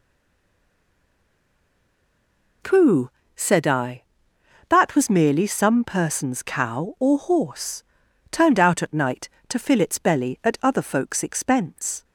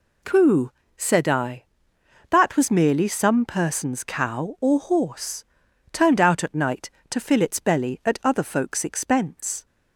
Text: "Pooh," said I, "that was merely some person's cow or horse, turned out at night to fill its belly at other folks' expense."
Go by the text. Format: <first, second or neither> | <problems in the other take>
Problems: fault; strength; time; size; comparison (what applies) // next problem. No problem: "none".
second | stays silent before the first word; strong; until 2.6 s; 2.6 s long